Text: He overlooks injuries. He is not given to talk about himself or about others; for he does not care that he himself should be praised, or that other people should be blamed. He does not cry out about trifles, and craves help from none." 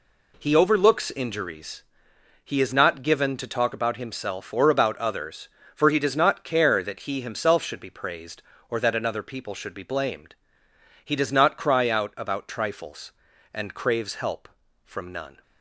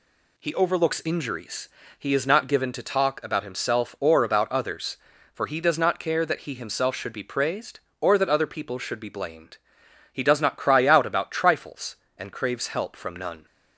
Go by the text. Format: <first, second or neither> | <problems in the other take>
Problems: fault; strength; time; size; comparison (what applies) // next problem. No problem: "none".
second | says "another" for "other"; at 8.9 s